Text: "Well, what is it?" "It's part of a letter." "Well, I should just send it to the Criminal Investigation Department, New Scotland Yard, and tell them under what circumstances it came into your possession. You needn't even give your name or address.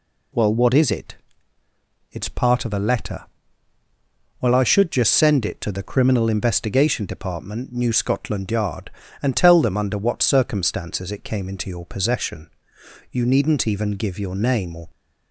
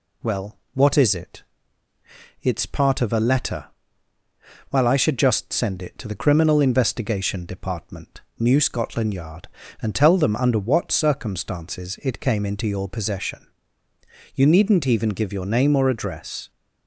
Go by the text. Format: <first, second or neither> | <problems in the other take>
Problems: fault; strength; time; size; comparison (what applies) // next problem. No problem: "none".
second | stops before "address"; at 14.9 s